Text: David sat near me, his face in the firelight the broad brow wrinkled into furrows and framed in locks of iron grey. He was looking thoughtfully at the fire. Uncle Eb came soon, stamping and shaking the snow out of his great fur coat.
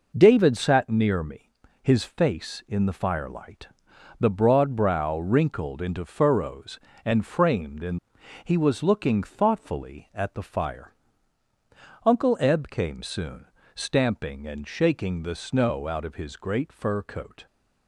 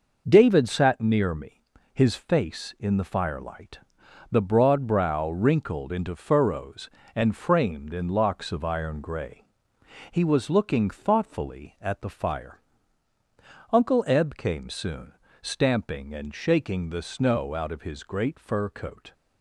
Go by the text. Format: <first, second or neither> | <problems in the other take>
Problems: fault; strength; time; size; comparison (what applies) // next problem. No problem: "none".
second | pauses between "firelight" and "the"; noticeable; at 3.6 s; 0.54 s long; noticeable in the second // skips "locks of iron grey"; at 8.2 s